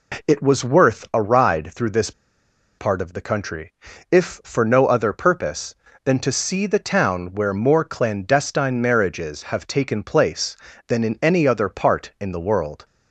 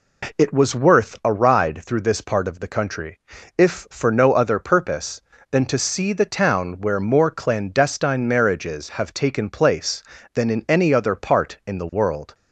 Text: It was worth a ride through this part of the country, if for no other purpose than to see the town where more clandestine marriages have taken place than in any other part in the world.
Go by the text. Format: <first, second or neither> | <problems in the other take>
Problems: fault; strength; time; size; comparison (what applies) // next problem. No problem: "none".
second | pauses between "this" and "part"; noticeable; at 2.1 s; 0.67 s long